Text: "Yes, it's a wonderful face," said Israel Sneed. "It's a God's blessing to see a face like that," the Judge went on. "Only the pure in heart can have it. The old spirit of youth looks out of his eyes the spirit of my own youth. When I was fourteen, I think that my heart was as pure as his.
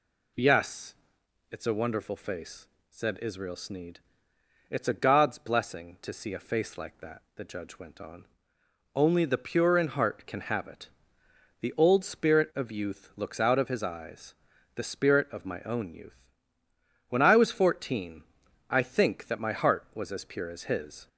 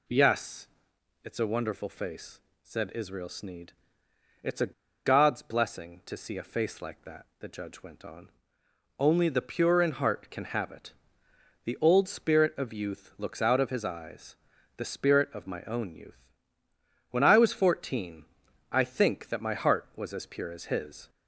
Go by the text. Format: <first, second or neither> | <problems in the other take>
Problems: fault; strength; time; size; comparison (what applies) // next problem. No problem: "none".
first | pauses between "a" and "God's"; slight; at 4.7 s; 0.32 s long // pauses between "eyes" and "the"; at 14.3 s; 0.40 s long; also in the first